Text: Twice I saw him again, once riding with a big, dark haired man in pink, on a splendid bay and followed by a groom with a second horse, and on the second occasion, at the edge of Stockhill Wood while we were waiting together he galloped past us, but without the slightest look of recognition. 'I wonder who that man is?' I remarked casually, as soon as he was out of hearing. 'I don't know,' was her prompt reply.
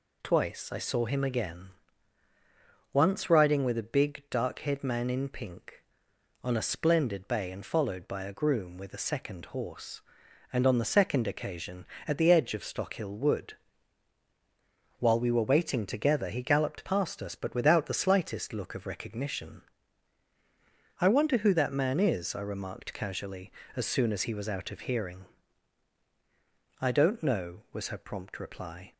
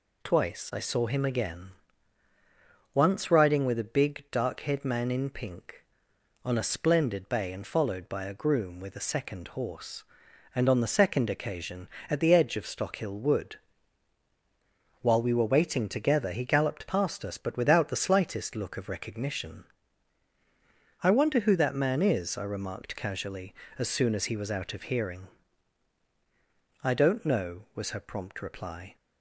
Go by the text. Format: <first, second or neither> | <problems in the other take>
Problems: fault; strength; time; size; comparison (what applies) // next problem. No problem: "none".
neither | pauses between "Wood" and "while"; strong; the same in both